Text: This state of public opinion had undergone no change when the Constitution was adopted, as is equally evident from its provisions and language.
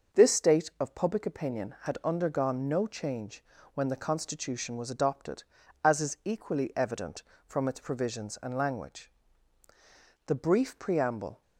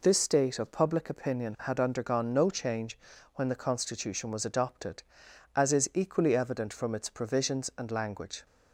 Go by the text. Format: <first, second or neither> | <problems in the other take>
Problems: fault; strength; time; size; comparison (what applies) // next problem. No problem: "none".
second | starts louder than the rest; until 1.2 s; 6.5 dB // pauses between "change" and "when"; slight; at 3.4 s; 0.32 s long; slight in the second // goes on to say "The brief preamble"; noticeable; from 10.2 s on; 1.1 s long